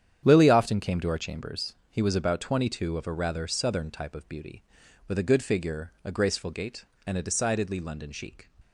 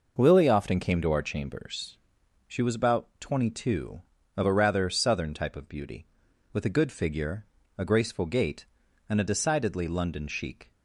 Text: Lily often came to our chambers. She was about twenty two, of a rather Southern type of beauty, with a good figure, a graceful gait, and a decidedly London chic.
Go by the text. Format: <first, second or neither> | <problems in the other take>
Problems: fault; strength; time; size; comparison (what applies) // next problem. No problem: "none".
second | starts louder than the rest; strong; until 1.2 s; 9 dB // says "He" for "She"; at 1.8 s